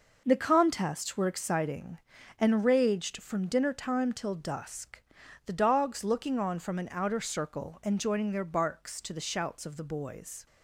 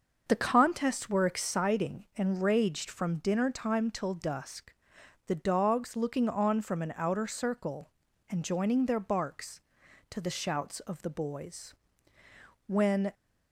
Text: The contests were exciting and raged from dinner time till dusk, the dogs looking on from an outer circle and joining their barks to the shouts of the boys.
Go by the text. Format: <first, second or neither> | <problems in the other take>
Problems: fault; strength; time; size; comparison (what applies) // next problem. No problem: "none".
first | starts louder than the rest; until 1.2 s; 6.5 dB // goes on to say "When"; slight; from 12.6 s on; 0.46 s long